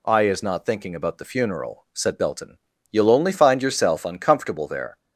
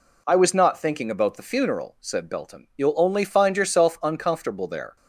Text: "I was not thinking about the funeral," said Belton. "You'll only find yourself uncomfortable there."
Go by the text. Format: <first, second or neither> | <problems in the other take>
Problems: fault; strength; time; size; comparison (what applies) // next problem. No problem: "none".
second | says "is" for "was"; at 0.2 s